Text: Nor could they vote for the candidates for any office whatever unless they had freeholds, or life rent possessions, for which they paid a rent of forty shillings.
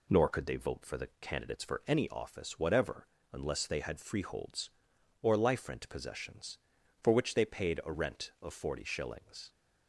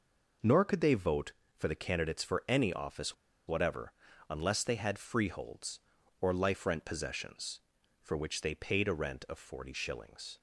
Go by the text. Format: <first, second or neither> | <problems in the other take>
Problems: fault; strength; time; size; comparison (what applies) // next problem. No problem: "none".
first | pauses between "office" and "whatever"; slight; at 3.1 s; 0.32 s long // pauses between "whatever" and "unless"; at 3.9 s; 0.38 s long; slight in the first